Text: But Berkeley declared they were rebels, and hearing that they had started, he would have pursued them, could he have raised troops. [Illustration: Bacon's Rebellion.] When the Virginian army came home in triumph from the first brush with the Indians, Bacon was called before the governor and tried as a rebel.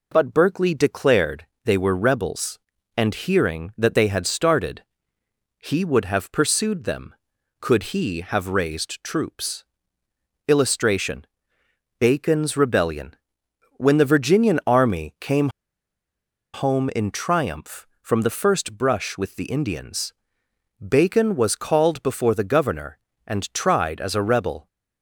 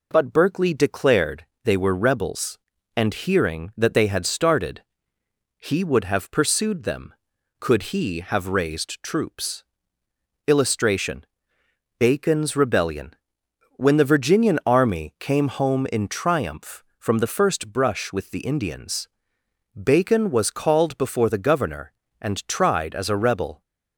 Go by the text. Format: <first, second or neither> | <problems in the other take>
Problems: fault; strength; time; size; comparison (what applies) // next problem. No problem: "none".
second | pauses between "declared" and "they"; slight; at 1.4 s; 0.18 s long; slight in the second // pauses between "came" and "home"; at 15.4 s; 1.0 s long